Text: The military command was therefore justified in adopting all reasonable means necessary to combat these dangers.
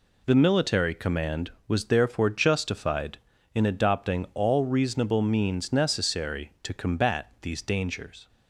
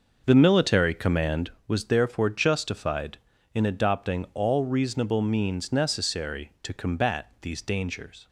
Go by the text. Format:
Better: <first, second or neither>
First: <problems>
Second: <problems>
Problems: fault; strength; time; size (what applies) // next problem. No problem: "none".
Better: first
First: none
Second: starts louder than the rest; noticeable; until 1.6 s; 6 dB